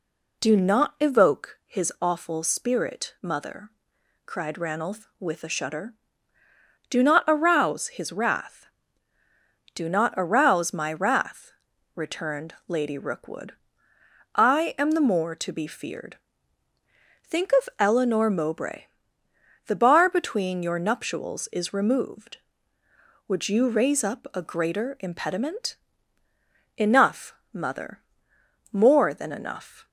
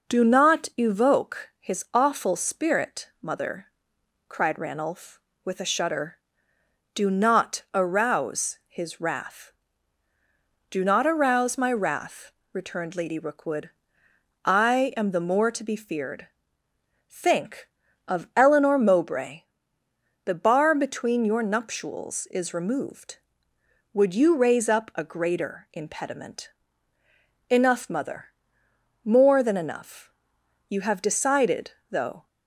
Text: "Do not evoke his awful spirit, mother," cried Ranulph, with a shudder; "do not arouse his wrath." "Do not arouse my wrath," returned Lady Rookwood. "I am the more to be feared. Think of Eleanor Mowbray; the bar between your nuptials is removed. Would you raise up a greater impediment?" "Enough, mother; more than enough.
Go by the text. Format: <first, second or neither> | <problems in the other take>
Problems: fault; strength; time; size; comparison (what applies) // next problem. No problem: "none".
first | goes on to say "You have decided though"; from 30.6 s on; 1.5 s long